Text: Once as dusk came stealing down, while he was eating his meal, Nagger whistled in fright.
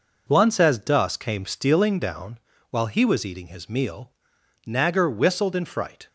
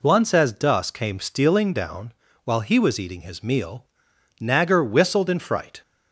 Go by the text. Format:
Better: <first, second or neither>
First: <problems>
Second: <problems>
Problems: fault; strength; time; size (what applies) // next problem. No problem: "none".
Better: second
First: gets quieter; throughout; 7 dB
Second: none